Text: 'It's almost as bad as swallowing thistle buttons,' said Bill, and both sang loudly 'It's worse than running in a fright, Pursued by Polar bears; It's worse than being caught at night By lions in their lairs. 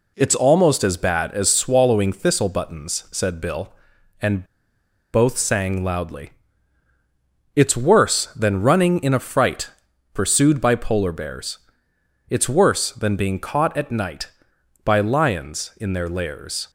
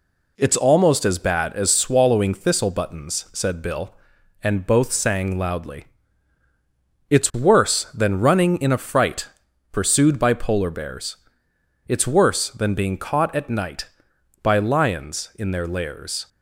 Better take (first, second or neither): second